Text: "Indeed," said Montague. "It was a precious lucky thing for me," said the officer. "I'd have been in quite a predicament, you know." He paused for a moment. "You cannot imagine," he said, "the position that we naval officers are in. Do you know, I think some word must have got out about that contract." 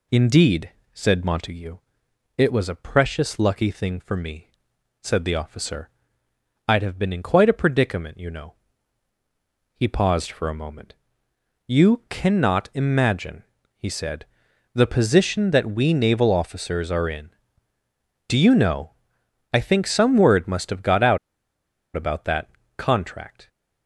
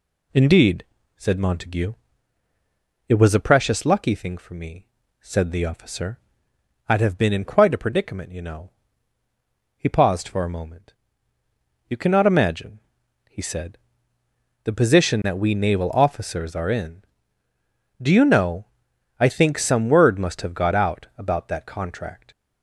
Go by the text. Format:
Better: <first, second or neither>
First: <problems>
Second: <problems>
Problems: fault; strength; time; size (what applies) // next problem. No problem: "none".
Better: second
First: pauses between "out" and "about"; noticeable; at 21.1 s; 0.77 s long // pauses between "that" and "contract"; slight; at 22.5 s; 0.26 s long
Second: none